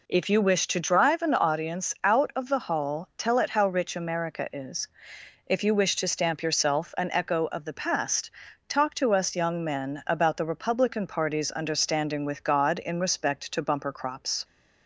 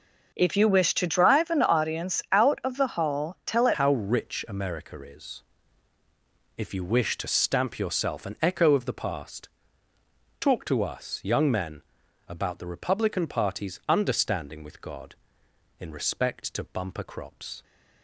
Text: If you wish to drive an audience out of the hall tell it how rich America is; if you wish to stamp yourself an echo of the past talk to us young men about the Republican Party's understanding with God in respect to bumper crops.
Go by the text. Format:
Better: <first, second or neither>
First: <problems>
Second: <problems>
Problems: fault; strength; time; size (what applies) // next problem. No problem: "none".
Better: first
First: pauses between "past" and "talk"; at 8.3 s; 0.38 s long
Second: changes voice at "how"; from 3.7 s on; 13.9 s long // pauses between "past" and "talk"; noticeable; at 9.4 s; 0.94 s long // pauses between "men" and "about"; at 11.8 s; 0.44 s long